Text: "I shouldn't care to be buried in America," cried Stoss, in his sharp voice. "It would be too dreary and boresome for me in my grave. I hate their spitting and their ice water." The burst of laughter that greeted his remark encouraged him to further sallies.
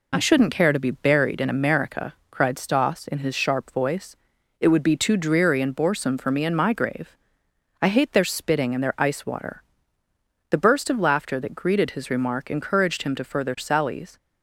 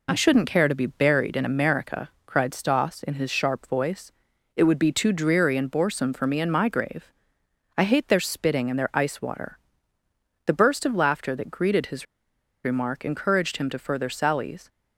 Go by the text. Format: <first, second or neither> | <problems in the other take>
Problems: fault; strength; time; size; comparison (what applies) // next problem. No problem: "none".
first | pauses between "his" and "remark"; noticeable; at 12.0 s; 0.60 s long